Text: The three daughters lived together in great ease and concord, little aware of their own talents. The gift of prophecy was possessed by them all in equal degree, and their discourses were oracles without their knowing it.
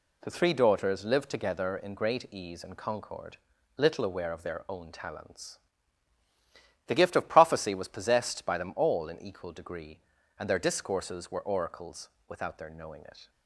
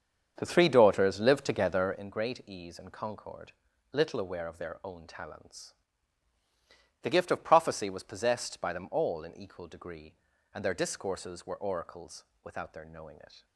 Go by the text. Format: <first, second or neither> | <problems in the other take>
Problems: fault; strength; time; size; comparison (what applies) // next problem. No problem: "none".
first | starts louder than the rest; until 2.1 s; 7 dB // pauses between "oracles" and "without"; slight; at 12.2 s; 0.18 s long; slight in the first